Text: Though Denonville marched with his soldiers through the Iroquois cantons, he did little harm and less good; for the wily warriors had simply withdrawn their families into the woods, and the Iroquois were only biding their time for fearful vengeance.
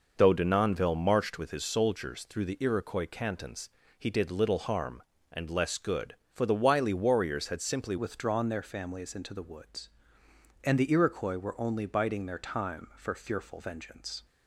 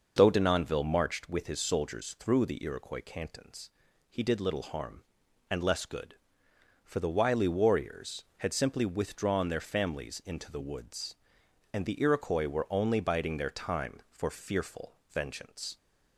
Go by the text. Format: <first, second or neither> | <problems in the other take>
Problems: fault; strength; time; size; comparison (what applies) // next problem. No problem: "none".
second | changes voice at "withdrawn"; from 7.9 s on; 6.3 s long